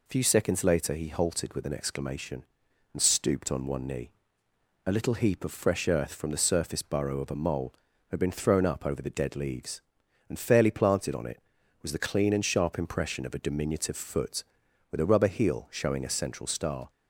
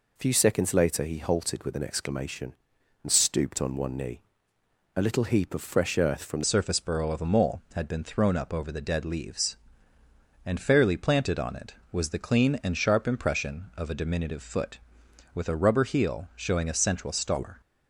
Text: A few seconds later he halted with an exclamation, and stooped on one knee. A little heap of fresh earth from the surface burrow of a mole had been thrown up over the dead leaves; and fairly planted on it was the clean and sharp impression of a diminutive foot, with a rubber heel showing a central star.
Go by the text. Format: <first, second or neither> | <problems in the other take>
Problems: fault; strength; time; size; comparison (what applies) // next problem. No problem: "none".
first | changes voice at "surface"; from 6.4 s on; 11.2 s long